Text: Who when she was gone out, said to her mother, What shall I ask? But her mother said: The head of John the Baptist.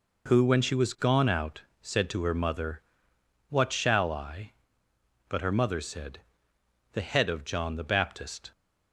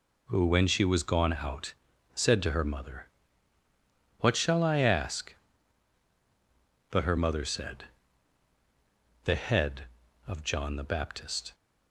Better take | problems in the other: second | skips "ask"; at 4.8 s

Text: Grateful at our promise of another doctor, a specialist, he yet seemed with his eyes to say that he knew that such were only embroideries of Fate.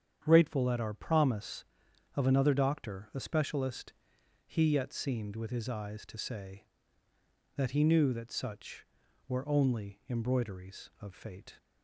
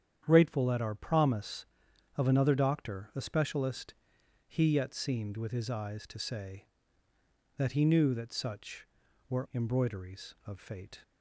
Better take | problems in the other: first | starts louder than the rest; strong; until 1.2 s; 9 dB; strong in the first // skips "only"; at 9.4 s

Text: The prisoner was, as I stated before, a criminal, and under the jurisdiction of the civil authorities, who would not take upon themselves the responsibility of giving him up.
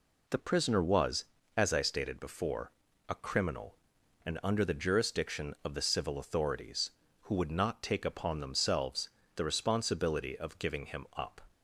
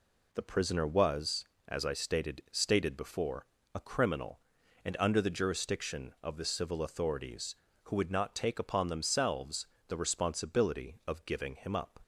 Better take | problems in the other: first | says "stated" twice; at 2.5 s // pauses between "themselves" and "the"; slight; at 9.6 s; 0.22 s long; slight in the first

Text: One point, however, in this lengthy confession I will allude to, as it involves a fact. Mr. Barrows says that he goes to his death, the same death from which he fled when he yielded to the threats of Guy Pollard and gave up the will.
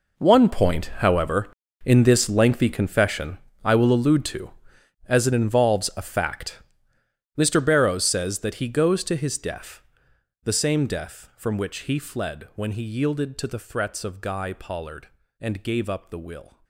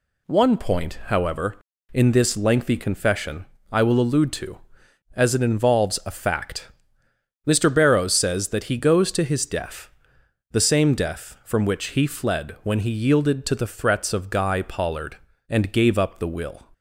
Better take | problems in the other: second | gets quieter; strong; throughout; 14.5 dB // pauses between "confession" and "I"; slight; at 3.3 s; 0.26 s long; slight in the second

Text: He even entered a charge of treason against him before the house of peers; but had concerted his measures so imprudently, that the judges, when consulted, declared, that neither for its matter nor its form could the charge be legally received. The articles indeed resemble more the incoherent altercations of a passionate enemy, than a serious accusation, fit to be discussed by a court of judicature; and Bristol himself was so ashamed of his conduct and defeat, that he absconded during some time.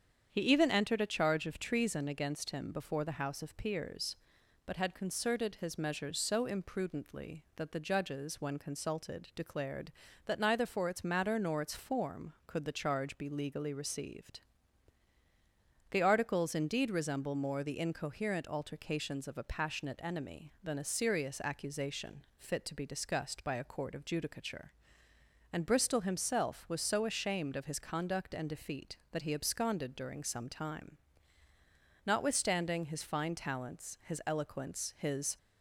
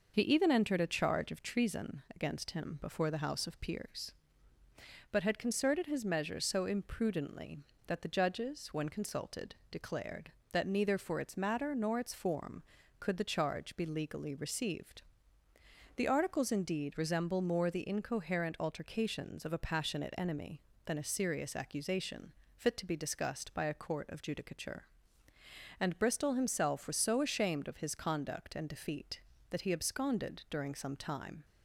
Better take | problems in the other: second | starts louder than the rest; strong; until 1.3 s; 8 dB // goes on to say "Notwithstanding his fine talents his eloquence his"; strong; from 32.0 s on; 3.3 s long

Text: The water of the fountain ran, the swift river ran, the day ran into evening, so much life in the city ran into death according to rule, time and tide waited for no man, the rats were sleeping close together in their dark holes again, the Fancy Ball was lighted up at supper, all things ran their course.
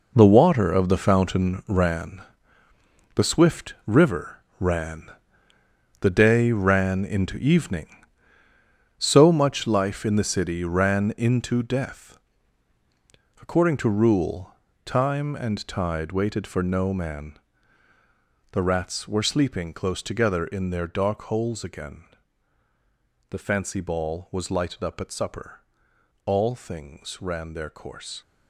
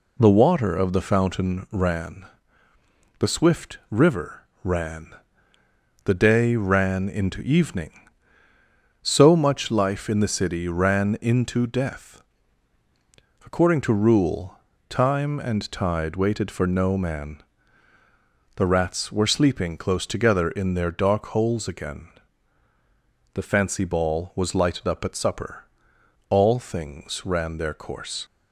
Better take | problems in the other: second | gets quieter; strong; throughout; 11 dB // pauses between "river" and "ran"; slight; at 4.4 s; 0.18 s long; slight in the second // pauses between "death" and "according"; at 12.1 s; 1.2 s long; also in the second

